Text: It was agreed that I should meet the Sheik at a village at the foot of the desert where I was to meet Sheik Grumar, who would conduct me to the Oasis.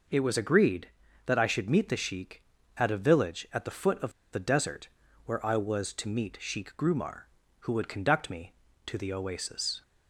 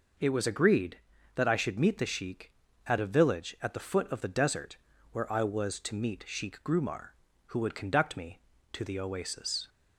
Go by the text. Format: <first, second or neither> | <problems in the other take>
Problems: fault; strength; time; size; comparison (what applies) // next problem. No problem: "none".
second | pauses between "of" and "the"; slight; at 4.1 s; 0.20 s long // pauses between "desert" and "where"; slight; at 4.8 s; 0.36 s long; slight in the second